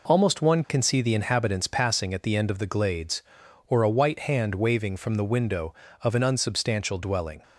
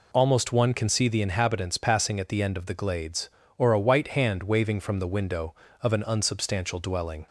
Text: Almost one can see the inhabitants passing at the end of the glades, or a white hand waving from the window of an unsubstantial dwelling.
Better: neither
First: none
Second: none

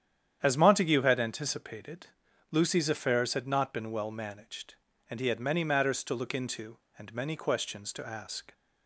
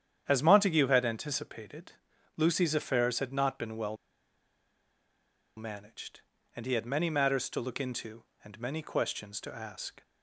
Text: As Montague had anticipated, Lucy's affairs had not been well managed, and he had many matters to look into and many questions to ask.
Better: first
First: starts louder than the rest; strong; until 1.4 s; 9 dB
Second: starts louder than the rest; strong; until 1.2 s; 9 dB // pauses between "well" and "managed"; strong; at 3.9 s; 1.6 s long

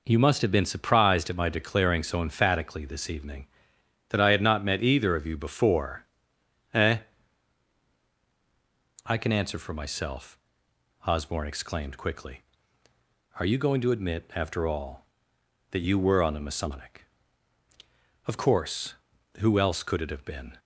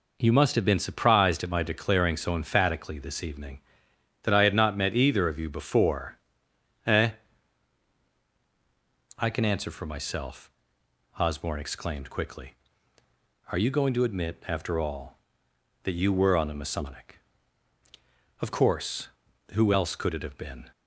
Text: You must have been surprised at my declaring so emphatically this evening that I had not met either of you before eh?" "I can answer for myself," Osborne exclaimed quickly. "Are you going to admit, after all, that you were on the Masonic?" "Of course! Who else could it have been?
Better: neither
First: pauses between "before" and "eh"; noticeable; at 6.0 s; 0.68 s long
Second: pauses between "before" and "eh"; noticeable; at 6.1 s; 0.68 s long

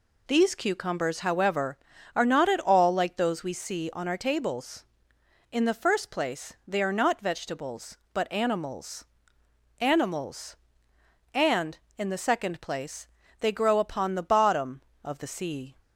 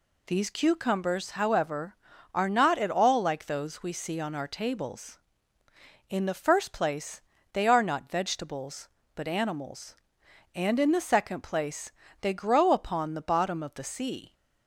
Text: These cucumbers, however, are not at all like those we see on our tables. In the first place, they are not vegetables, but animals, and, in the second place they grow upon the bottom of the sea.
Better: second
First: says "animals" twice; at 9.7 s // pauses between "place" and "they"; slight; at 13.0 s; 0.34 s long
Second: pauses between "place" and "they"; slight; at 11.9 s; 0.30 s long

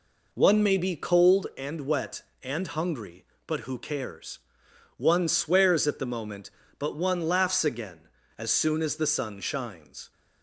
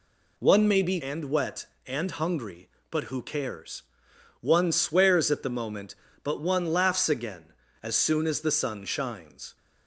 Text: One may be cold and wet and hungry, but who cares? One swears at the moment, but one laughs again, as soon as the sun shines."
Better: first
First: none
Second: skips "cold"; at 1.0 s

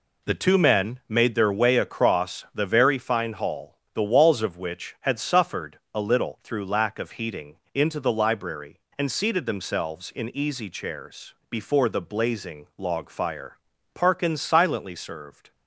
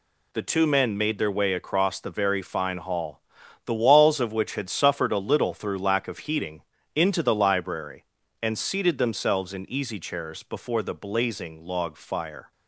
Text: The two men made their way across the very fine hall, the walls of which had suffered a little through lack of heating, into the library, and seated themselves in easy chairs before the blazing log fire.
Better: second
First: pauses between "suffered" and "a"; slight; at 5.7 s; 0.16 s long // pauses between "chairs" and "before"; slight; at 11.3 s; 0.16 s long // goes on to say "Parkins silently served"; from 13.9 s on; 1.5 s long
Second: none

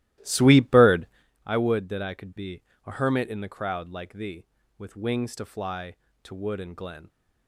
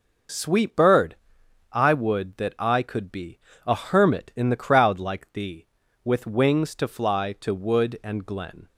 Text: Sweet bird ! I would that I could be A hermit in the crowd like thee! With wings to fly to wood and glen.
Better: second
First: starts louder than the rest; strong; until 1.3 s; 15.5 dB // pauses between "be" and "A"; slight; at 2.6 s; 0.24 s long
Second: pauses between "be" and "A"; slight; at 3.3 s; 0.26 s long

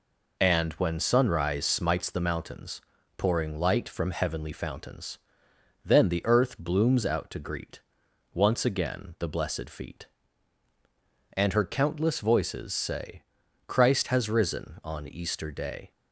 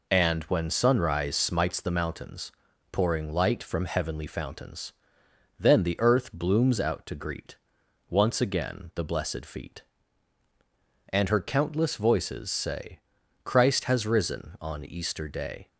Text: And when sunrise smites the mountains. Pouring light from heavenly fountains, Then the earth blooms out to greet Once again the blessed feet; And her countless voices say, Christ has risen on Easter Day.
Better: neither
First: pauses between "greet" and "Once"; noticeable; at 7.8 s; 0.52 s long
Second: pauses between "greet" and "Once"; noticeable; at 7.5 s; 0.52 s long

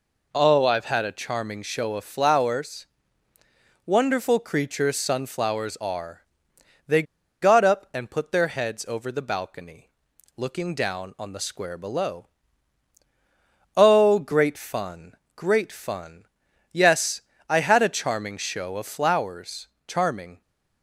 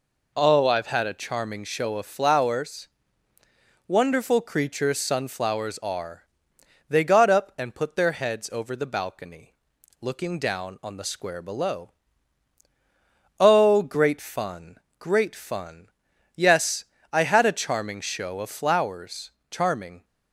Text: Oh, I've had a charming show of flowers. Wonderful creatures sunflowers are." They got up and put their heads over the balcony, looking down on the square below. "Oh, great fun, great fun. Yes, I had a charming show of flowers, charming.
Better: second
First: pauses between "They" and "got"; at 7.0 s; 0.39 s long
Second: none

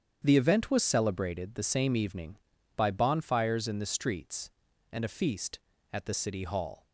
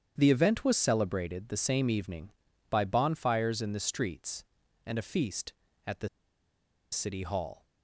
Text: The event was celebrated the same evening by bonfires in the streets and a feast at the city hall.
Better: first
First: starts louder than the rest; strong; until 1.2 s; 8.5 dB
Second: starts louder than the rest; strong; until 1.1 s; 8.5 dB // pauses between "the" and "city"; noticeable; at 6.0 s; 0.83 s long

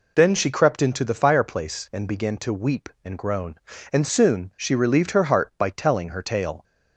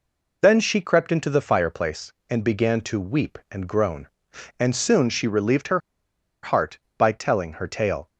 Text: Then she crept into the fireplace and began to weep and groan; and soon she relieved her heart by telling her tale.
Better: first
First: none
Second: pauses between "her" and "heart"; noticeable; at 5.7 s; 0.63 s long

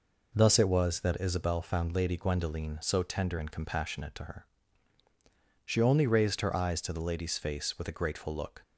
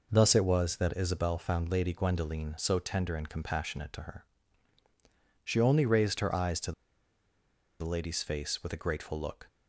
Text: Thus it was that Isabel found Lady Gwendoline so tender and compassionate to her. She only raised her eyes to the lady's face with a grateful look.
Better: first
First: none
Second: pauses between "to" and "the"; at 6.7 s; 1.0 s long

